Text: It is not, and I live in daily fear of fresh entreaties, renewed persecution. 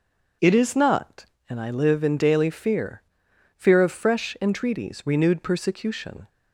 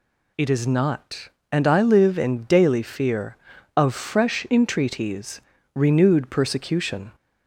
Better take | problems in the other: second | starts louder than the rest; until 1.6 s; 6.5 dB // says "fear" twice; at 3.5 s

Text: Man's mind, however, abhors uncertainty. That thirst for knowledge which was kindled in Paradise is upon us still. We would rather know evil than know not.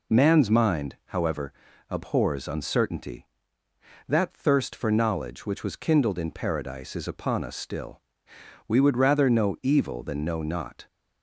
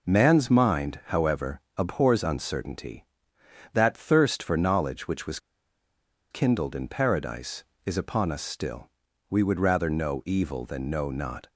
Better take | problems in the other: first | pauses between "was" and "kindled"; noticeable; at 5.3 s; 0.92 s long

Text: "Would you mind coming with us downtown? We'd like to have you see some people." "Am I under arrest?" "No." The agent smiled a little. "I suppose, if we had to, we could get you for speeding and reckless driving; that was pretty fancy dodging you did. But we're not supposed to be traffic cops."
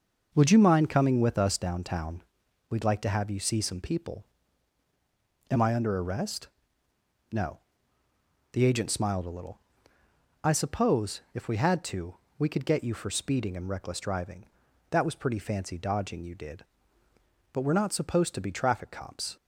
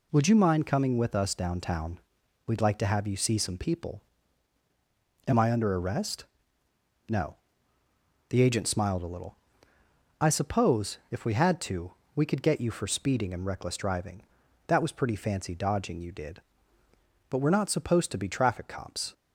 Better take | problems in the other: second | starts louder than the rest; noticeable; until 1.7 s; 6 dB

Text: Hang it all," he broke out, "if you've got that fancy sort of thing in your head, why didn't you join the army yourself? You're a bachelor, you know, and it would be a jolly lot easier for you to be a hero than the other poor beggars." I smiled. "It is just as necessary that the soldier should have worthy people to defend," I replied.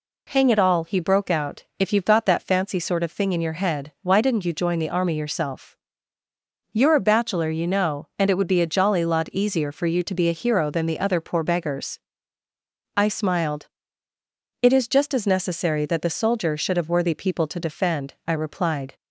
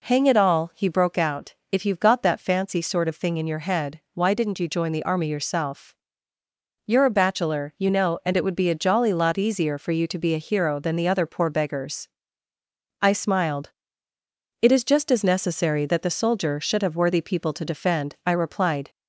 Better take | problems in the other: neither | none

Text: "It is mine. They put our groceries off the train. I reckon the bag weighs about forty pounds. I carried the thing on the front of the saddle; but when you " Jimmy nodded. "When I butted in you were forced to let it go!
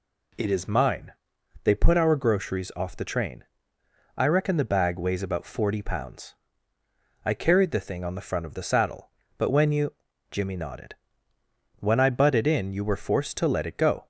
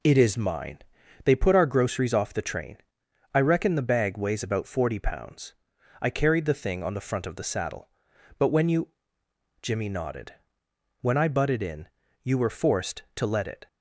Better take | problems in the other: first | pauses between "in" and "you"; slight; at 11.8 s; 0.36 s long // stops before "go"; at 13.6 s

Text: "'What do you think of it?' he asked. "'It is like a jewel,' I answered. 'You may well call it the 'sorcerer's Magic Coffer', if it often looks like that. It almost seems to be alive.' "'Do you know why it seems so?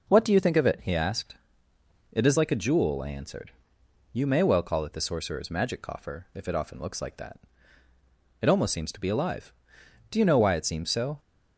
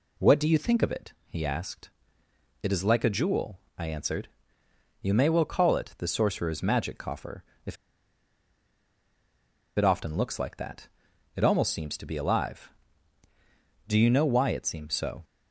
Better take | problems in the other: first | pauses between "if" and "it"; strong; at 7.7 s; 2.0 s long

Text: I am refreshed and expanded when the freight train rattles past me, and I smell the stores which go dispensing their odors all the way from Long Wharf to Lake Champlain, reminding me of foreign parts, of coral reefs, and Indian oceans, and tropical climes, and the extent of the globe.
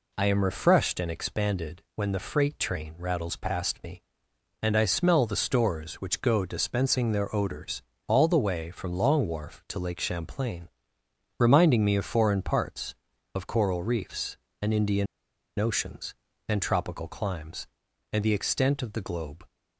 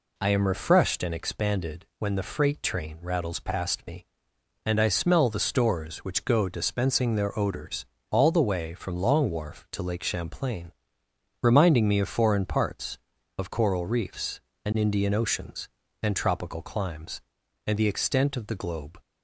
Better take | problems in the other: second | pauses between "odors" and "all"; slight; at 7.8 s; 0.26 s long; slight in the second // pauses between "Indian" and "oceans"; noticeable; at 15.0 s; 0.53 s long

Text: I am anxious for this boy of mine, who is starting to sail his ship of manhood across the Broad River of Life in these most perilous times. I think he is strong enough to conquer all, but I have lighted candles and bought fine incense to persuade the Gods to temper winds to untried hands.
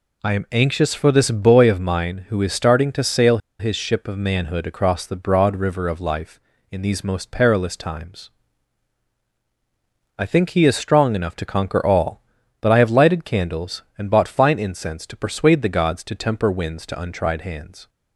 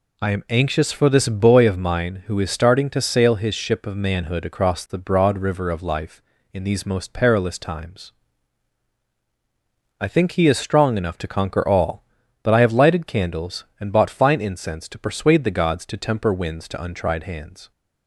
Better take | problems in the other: second | pauses between "sail" and "his"; slight; at 3.3 s; 0.21 s long

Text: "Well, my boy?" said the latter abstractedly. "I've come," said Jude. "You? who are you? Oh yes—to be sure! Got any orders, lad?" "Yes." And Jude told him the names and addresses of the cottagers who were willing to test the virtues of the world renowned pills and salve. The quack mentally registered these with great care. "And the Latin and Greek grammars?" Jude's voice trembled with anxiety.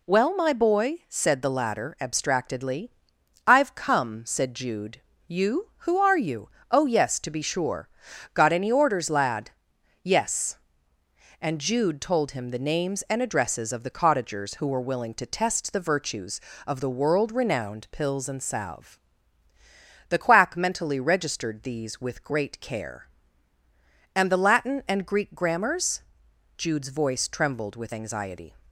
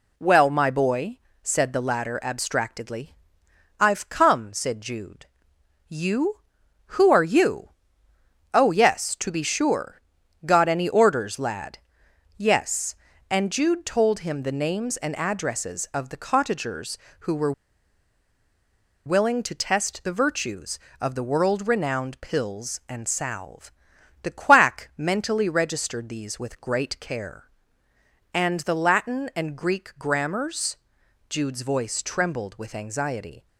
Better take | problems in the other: first | pauses between "were" and "willing"; strong; at 17.5 s; 1.5 s long

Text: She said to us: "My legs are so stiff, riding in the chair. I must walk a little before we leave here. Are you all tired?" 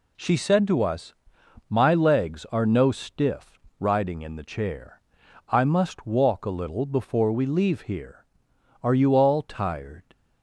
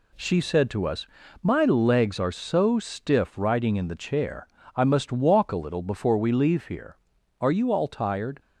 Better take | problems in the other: second | says "no" for "so"; at 2.6 s

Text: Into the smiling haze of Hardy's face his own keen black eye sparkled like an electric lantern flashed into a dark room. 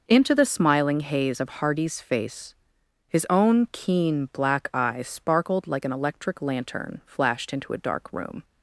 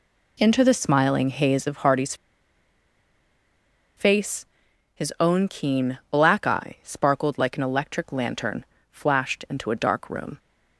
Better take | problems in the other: first | pauses between "Hardy's" and "face"; strong; at 2.1 s; 1.8 s long // pauses between "face" and "his"; noticeable; at 4.4 s; 0.48 s long; noticeable in the first // pauses between "lantern" and "flashed"; slight; at 8.6 s; 0.26 s long

